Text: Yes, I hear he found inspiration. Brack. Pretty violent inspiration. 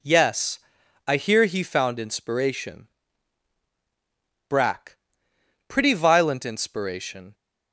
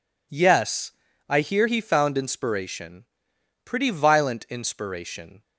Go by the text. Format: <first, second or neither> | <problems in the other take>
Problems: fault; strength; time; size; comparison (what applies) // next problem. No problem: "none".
first | skips "Brack"; at 3.3 s